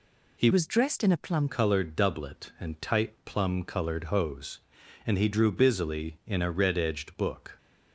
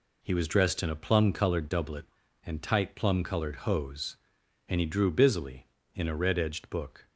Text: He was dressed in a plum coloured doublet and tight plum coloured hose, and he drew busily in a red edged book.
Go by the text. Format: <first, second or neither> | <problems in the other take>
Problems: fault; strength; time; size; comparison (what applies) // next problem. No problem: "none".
second | changes voice from "was" to "plum"; from 0.5 to 1.4 s; 0.9 s long